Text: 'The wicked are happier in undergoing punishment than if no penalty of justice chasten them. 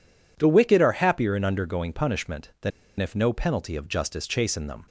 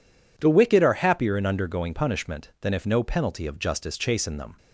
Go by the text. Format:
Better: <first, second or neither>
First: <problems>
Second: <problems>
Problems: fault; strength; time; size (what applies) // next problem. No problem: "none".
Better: second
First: pauses between "than" and "if"; slight; at 2.7 s; 0.29 s long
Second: none